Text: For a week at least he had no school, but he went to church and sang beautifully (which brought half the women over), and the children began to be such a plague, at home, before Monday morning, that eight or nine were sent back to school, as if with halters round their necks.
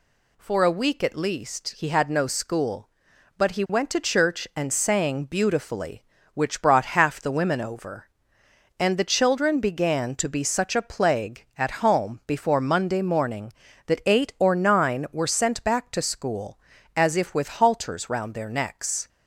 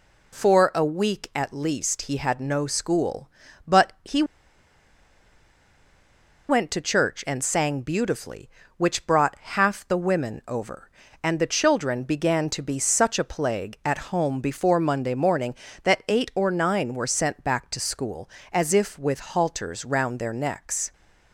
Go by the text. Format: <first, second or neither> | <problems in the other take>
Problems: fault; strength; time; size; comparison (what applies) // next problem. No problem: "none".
first | pauses between "he" and "went"; strong; at 4.2 s; 2.2 s long